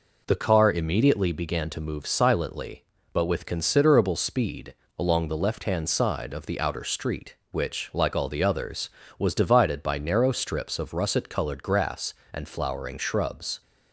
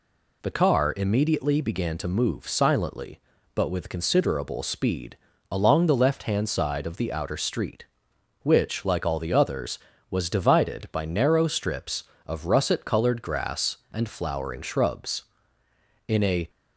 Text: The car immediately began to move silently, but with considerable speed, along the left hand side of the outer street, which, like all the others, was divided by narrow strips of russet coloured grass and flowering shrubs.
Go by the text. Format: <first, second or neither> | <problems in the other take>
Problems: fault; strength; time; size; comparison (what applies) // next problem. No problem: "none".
first | goes on to say "In a"; slight; from 16.0 s on; 0.42 s long